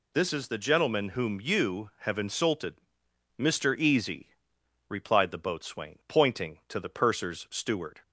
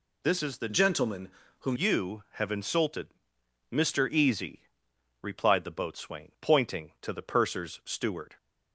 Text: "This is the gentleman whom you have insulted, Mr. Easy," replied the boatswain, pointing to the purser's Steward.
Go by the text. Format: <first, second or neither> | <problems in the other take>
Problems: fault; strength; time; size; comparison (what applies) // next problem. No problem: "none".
first | changes voice from "gentleman" to "whom"; from 0.7 to 1.7 s; 1.0 s long // pauses between "gentleman" and "whom"; slight; at 1.2 s; 0.30 s long